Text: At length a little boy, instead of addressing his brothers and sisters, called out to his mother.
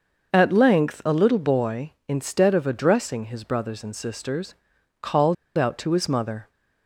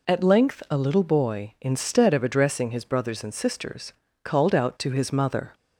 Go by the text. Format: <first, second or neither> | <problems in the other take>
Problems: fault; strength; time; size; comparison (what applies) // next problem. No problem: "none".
second | starts louder than the rest; noticeable; until 1.3 s; 6 dB // pauses between "called" and "out"; slight; at 5.3 s; 0.22 s long